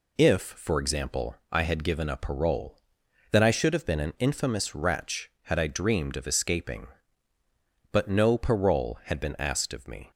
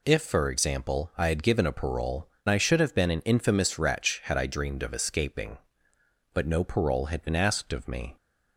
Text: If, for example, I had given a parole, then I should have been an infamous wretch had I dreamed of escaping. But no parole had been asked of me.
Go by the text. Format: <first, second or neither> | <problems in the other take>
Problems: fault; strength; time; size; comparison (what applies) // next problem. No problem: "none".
first | skips "then"; at 2.3 s